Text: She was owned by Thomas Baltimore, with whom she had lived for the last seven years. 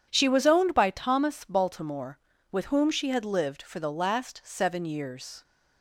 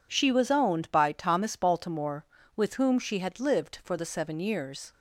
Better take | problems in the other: first | skips "last"; at 4.0 s

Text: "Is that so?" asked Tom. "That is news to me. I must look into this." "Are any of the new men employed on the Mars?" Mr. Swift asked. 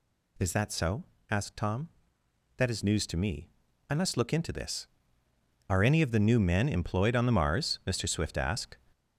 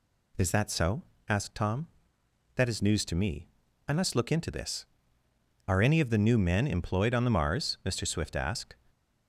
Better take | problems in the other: second | gets louder; noticeable; throughout; 5 dB

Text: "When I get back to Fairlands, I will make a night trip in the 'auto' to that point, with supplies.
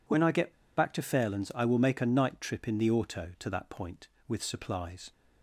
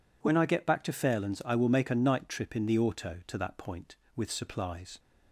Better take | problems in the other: second | pauses between "get" and "back"; slight; at 0.5 s; 0.24 s long

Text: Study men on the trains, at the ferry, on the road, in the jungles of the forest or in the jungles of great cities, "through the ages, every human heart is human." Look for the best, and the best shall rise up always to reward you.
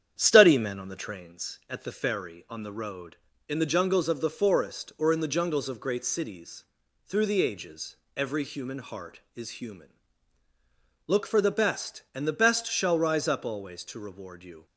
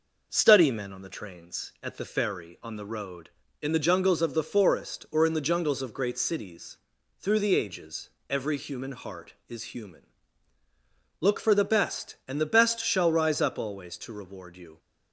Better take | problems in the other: second | starts louder than the rest; strong; until 1.3 s; 9 dB

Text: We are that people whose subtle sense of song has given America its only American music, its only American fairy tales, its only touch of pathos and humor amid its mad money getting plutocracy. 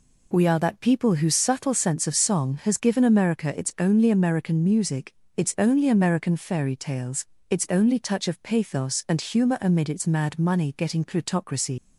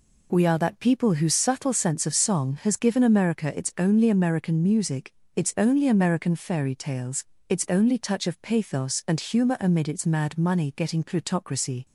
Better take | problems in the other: second | leaves "plutocracy" unfinished; at 11.7 s; 80 ms

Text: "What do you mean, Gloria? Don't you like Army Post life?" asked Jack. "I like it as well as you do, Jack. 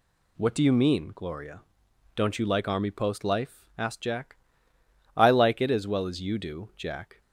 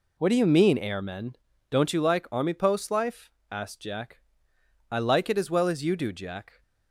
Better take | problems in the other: first | says "Airmen" for "Gloria"; at 0.7 s

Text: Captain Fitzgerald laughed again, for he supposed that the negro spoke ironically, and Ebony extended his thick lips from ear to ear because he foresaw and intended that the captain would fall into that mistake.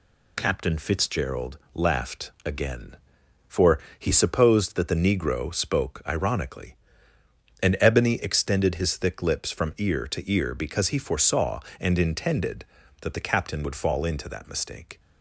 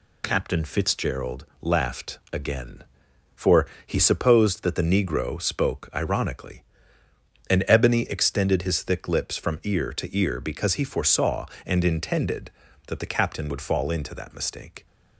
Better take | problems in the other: neither | pauses between "Fitzgerald" and "laughed"; slight; the same in both // pauses between "laughed" and "again"; slight; the same in both // pauses between "for" and "he"; slight; the same in both

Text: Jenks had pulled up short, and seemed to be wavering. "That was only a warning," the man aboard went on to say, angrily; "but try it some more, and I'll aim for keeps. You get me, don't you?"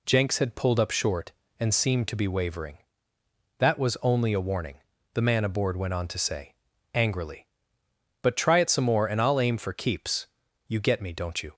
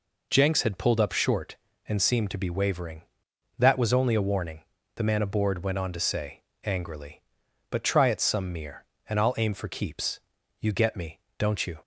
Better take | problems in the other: first | says "mere" for "more"; at 8.5 s

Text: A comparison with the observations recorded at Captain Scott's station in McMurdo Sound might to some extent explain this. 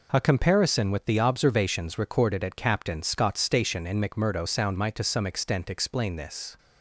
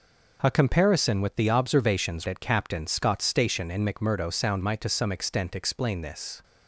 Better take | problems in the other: first | skips "recorded"; at 2.2 s

